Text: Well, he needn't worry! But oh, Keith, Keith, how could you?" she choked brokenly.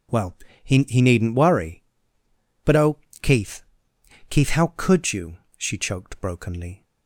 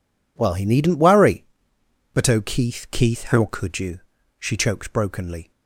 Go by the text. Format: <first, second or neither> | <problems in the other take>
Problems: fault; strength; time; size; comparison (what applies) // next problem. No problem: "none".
second | says "he" twice; at 0.8 s